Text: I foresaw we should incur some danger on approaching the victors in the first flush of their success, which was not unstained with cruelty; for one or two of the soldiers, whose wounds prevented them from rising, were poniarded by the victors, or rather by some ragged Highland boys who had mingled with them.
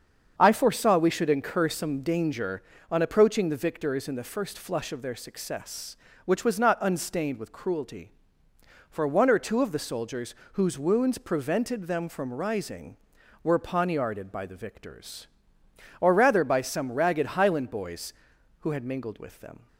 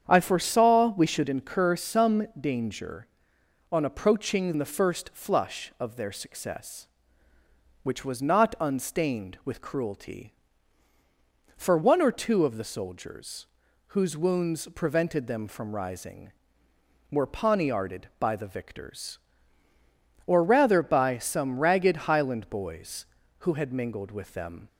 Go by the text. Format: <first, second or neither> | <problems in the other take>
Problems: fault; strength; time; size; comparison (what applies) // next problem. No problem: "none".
first | starts louder than the rest; strong; until 1.0 s; 8 dB; strong in the first // skips "the victors in"; at 4.5 s